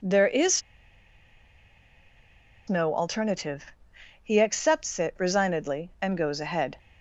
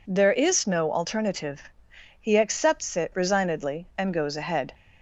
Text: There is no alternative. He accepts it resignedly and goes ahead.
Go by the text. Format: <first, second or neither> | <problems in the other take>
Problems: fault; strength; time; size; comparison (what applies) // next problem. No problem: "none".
second | pauses between "is" and "no"; strong; at 0.6 s; 2.0 s long